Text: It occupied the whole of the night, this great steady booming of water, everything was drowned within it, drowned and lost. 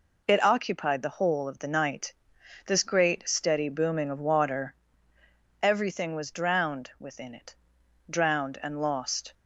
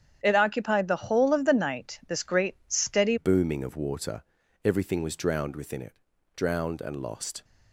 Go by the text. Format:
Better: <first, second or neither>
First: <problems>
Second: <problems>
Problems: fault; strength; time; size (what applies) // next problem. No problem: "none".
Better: first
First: none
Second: starts louder than the rest; strong; until 1.2 s; 9.5 dB // changes voice at "booming"; from 3.1 s on; 4.3 s long